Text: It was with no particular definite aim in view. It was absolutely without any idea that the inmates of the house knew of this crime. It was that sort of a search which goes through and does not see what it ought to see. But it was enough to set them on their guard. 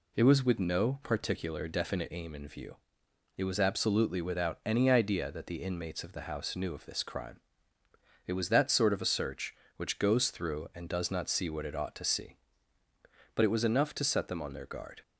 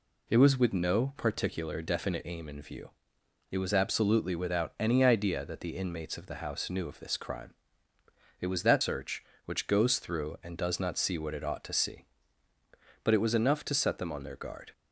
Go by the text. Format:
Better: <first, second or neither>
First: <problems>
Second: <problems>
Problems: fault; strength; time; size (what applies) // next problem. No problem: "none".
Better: first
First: none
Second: skips "sort of a"; at 8.8 s